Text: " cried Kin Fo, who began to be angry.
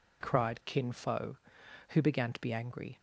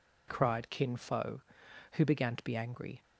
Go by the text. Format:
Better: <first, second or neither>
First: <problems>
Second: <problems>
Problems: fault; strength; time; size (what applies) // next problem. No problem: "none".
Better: neither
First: none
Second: none